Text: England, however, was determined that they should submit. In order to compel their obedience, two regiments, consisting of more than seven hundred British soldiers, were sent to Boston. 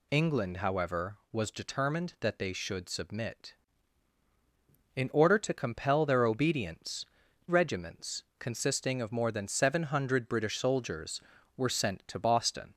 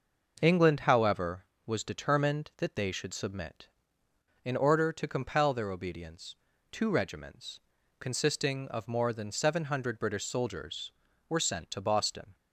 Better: second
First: skips "two"; at 7.2 s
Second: none

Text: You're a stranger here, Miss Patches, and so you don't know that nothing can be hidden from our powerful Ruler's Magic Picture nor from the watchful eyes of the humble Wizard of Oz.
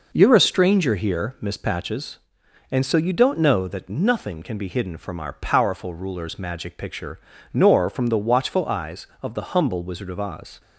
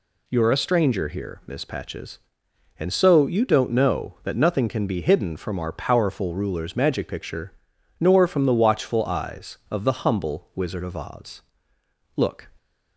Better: first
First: pauses between "Picture" and "nor"; slight; at 7.1 s; 0.36 s long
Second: pauses between "Picture" and "nor"; noticeable; at 7.5 s; 0.46 s long // goes on to say "Look"; slight; from 12.1 s on; 0.32 s long

